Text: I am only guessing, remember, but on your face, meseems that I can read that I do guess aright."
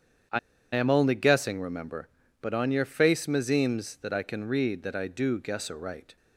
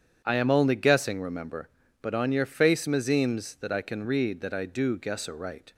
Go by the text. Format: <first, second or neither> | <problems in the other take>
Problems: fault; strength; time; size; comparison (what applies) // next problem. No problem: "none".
second | starts louder than the rest; strong; until 1.6 s; 8.5 dB; strong in the second // pauses between "I" and "am"; slight; at 0.3 s; 0.34 s long